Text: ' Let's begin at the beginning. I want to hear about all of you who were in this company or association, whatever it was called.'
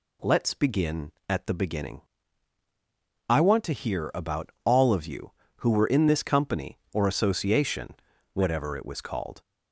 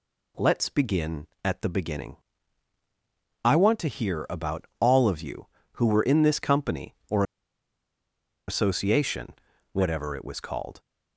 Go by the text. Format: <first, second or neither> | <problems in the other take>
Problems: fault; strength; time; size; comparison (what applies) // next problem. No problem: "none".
first | pauses between "or" and "association"; at 7.2 s; 1.2 s long